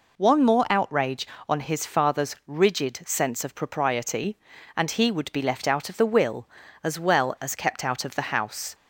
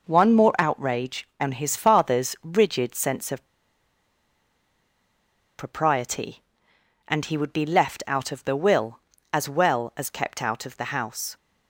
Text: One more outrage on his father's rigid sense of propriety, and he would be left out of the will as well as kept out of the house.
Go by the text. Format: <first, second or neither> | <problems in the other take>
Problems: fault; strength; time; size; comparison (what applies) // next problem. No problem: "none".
first | pauses between "of" and "propriety"; strong; at 3.4 s; 2.1 s long